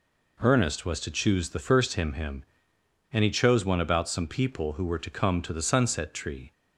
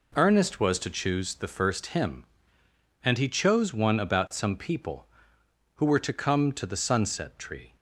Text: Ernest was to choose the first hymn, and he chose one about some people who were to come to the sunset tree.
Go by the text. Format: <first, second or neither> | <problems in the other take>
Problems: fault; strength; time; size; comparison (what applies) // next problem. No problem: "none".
second | says "hymn" twice; at 2.1 s